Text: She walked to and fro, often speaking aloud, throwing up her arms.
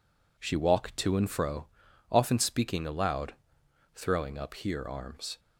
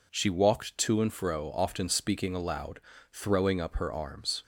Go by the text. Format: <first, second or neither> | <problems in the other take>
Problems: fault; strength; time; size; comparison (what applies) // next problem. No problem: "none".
second | says "here" for "her"; at 4.5 s